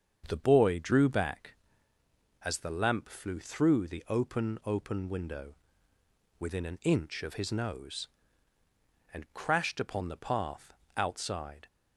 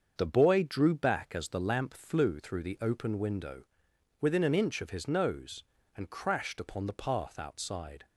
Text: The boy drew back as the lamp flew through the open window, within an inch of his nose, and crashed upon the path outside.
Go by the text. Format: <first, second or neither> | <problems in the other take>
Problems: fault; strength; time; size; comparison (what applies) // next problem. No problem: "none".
second | starts louder than the rest; strong; until 1.2 s; 7 dB; also in the second // says "open" twice; at 4.6 s // pauses between "path" and "outside"; slight; at 10.7 s; 0.24 s long